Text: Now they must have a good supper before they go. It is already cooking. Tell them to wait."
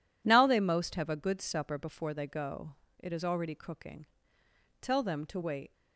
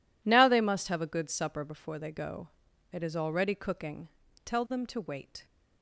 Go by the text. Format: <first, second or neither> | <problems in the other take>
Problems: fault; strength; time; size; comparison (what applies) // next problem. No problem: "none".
second | says "most" for "must"; at 0.5 s